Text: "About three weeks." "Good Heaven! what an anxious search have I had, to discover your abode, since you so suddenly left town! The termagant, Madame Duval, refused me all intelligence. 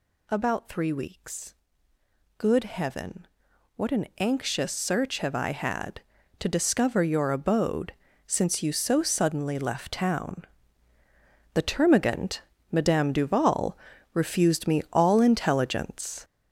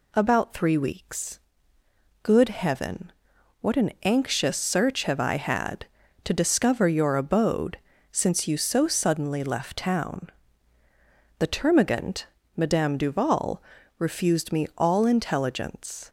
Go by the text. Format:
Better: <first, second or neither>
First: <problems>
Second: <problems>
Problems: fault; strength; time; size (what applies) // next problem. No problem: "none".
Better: second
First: gets louder; strong; throughout; 7 dB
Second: none